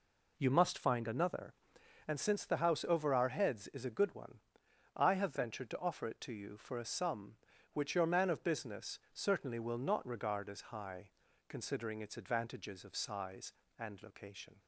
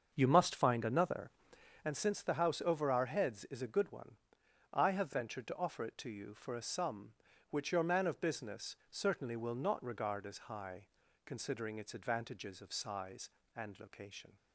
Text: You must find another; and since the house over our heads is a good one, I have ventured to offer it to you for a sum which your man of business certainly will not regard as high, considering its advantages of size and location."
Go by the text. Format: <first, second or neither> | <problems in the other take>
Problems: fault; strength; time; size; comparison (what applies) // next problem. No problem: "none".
first | starts louder than the rest; until 1.9 s; 7 dB